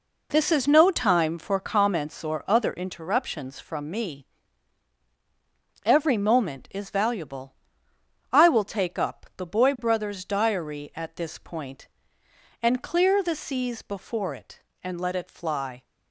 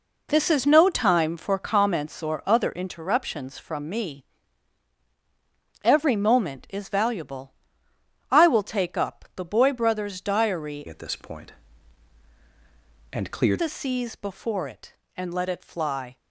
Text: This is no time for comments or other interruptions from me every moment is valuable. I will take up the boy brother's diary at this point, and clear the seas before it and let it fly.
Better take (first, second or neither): first